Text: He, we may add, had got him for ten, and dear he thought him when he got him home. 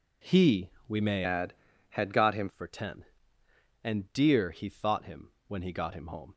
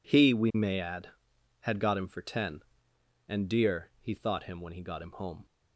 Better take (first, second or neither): second